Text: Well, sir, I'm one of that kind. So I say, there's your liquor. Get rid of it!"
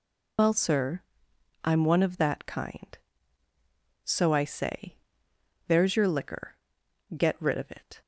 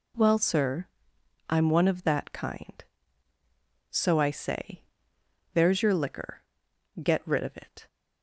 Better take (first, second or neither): second